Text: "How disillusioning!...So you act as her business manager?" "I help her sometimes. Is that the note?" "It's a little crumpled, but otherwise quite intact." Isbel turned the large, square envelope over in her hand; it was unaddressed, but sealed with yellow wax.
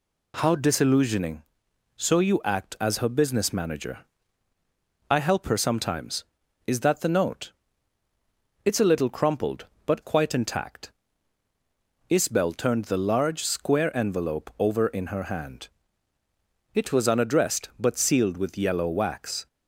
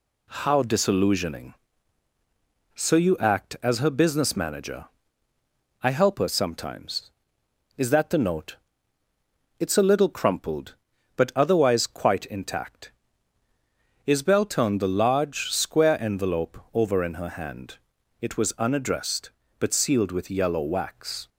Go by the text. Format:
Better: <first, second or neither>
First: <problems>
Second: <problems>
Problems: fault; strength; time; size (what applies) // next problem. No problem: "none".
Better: second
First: skips "otherwise"; at 10.0 s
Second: none